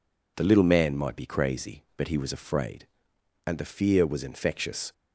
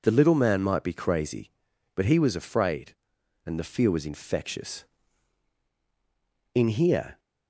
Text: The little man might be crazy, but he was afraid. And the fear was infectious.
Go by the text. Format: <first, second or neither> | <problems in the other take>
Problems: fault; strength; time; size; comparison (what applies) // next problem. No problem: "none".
first | goes on to say "In here"; noticeable; from 6.5 s on; 0.66 s long